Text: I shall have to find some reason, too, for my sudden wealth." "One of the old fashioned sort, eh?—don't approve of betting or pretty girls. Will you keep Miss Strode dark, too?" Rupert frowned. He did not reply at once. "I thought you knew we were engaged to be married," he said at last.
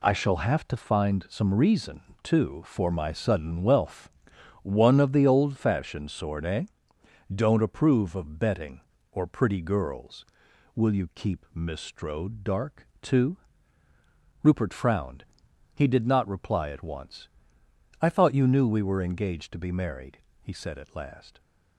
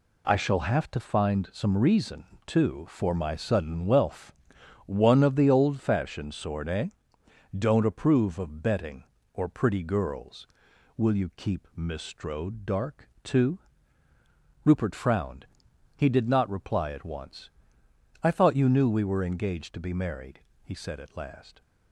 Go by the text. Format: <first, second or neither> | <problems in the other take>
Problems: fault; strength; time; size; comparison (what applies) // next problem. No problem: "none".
neither | none